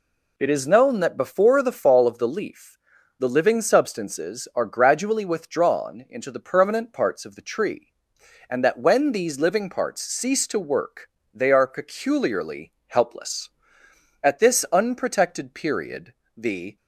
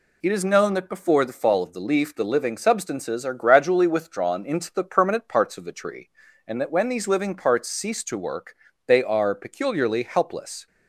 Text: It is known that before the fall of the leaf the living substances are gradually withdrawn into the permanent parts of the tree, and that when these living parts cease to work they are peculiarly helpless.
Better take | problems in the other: second | pauses between "leaf" and "the"; at 2.7 s; 0.40 s long // pauses between "work" and "they"; slight; at 11.0 s; 0.24 s long; slight in the second // pauses between "peculiarly" and "helpless"; slight; at 12.7 s; 0.16 s long // goes on to say "At this unprotected period the"; strong; from 14.2 s on; 2.5 s long

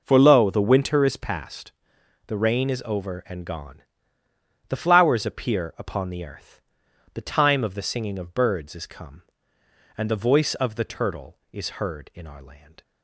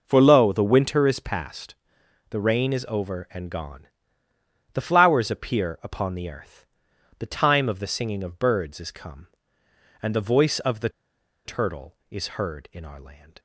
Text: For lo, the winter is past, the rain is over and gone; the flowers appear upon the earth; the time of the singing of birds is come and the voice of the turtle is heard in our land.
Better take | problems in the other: first | pauses between "the" and "turtle"; noticeable; at 10.8 s; 0.55 s long

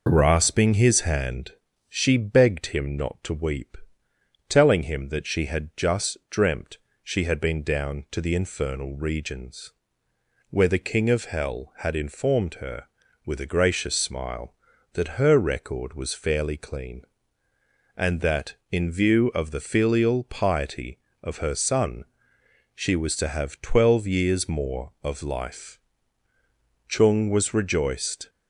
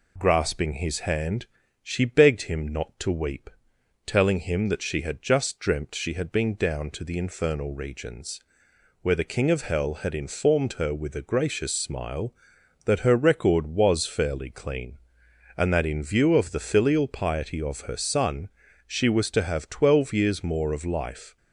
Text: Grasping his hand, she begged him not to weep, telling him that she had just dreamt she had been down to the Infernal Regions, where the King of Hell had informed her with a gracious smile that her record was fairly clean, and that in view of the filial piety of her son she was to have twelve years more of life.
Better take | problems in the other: second | pauses between "dreamt" and "she"; slight; at 6.7 s; 0.26 s long // pauses between "son" and "she"; noticeable; at 22.0 s; 0.68 s long; also in the second // goes on to say "Chung was rejoiced"; from 26.8 s on; 1.4 s long

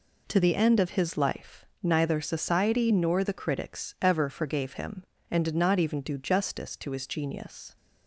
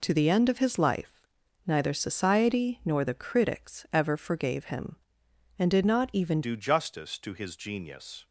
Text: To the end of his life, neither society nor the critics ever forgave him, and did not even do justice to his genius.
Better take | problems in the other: first | changes voice at "do"; from 6.4 s on; 1.8 s long

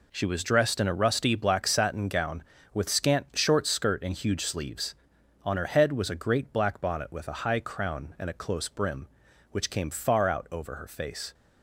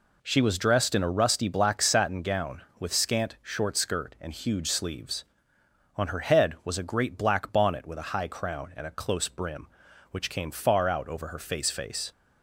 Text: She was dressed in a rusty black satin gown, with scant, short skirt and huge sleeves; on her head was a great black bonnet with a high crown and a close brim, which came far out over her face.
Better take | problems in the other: first | says "face" twice; at 11.7 s

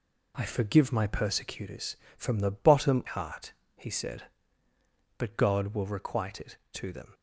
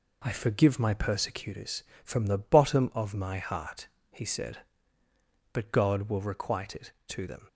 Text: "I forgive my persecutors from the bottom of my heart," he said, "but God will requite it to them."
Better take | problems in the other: second | skips "of my"; at 3.0 s

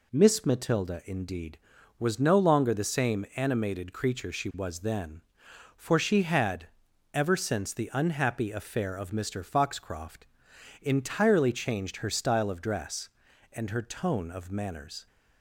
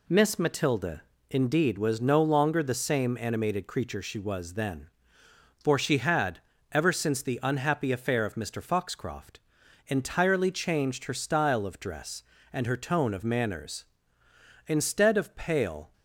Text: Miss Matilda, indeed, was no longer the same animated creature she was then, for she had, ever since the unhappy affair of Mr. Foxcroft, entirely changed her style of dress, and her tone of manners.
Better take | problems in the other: first | goes on to say "Instead of pale"; noticeable; from 14.6 s on; 1.2 s long

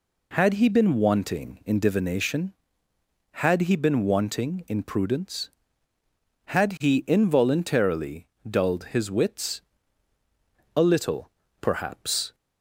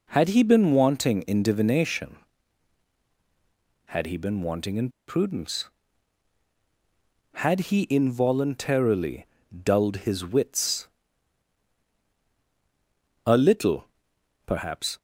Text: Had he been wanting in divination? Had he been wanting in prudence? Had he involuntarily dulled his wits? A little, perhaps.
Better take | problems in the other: first | pauses between "in" and "prudence"; slight; at 4.8 s; 0.19 s long // pauses between "involuntarily" and "dulled"; at 9.2 s; 0.38 s long; slight in the first

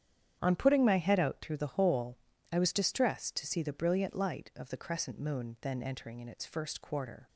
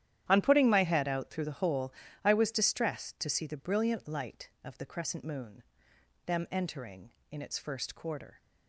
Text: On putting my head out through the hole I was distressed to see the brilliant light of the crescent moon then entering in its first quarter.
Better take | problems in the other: first | starts louder than the rest; strong; until 1.3 s; 11 dB; strong in the first // pauses between "hole" and "I"; slight; at 1.9 s; 0.30 s long; slight in the first // says "them" for "then"; at 6.2 s

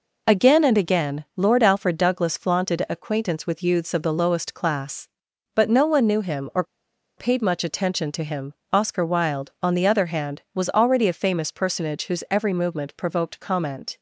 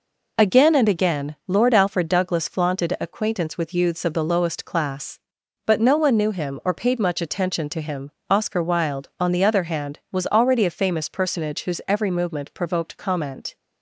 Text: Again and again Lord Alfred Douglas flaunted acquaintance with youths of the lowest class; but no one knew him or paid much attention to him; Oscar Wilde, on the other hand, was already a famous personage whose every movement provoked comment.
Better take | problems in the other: second | pauses between "or" and "paid"; noticeable; at 6.6 s; 0.54 s long

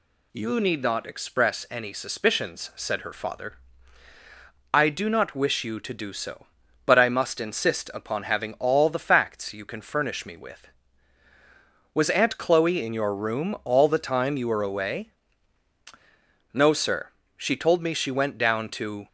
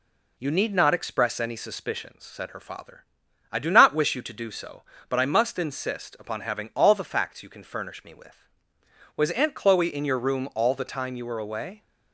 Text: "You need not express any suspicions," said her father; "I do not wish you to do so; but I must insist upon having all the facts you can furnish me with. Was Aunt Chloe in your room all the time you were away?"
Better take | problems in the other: second | goes on to say "No sir she told me she went down to"; strong; from 16.5 s on; 2.5 s long

